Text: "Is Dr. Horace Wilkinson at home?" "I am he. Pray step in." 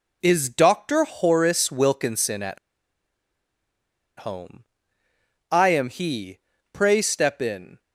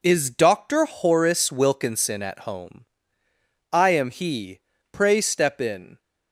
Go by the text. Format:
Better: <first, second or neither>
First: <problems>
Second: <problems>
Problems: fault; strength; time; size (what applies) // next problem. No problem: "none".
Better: second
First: pauses between "at" and "home"; strong; at 2.5 s; 1.6 s long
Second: none